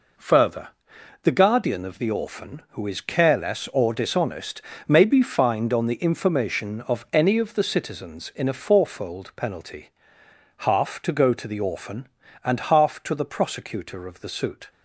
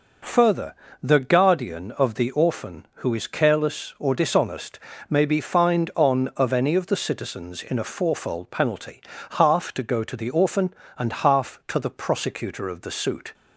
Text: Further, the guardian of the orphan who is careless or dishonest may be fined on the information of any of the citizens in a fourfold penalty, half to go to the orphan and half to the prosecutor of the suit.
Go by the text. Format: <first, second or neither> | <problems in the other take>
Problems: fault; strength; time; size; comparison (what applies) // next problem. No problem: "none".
first | pauses between "dishonest" and "may"; slight; at 4.7 s; 0.30 s long; slight in the first // skips "the information"; at 6.3 s